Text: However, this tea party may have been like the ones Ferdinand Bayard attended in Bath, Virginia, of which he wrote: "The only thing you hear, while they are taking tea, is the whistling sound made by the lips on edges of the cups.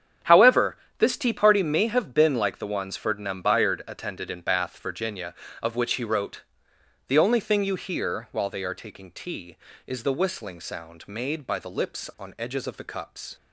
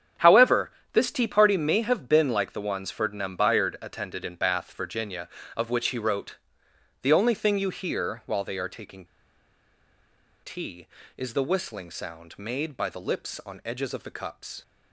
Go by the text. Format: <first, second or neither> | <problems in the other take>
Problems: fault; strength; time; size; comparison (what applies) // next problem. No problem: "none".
first | starts louder than the rest; strong; until 1.4 s; 8.5 dB; strong in the first // pauses between "taking" and "tea"; strong; at 9.0 s; 1.3 s long